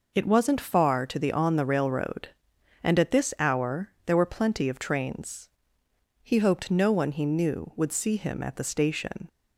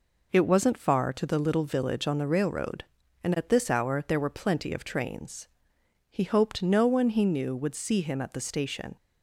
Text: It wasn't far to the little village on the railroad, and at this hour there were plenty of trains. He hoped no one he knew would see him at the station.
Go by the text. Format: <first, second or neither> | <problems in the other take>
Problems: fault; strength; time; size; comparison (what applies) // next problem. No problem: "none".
second | skips "little village"; at 1.3 s